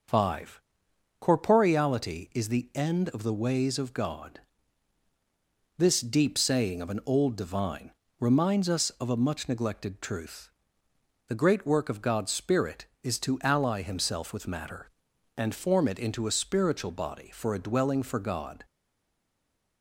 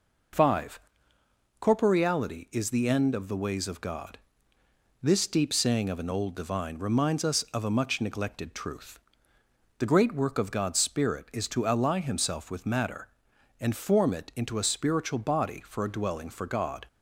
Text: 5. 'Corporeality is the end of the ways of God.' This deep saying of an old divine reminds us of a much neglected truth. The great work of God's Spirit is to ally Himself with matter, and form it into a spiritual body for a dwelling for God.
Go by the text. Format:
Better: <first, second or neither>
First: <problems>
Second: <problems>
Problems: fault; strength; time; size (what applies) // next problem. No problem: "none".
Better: second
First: starts louder than the rest; noticeable; until 1.6 s; 6 dB // pauses between "divine" and "reminds"; slight; at 7.9 s; 0.28 s long // stays silent after the last word; from 18.6 s on; 1.2 s long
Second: none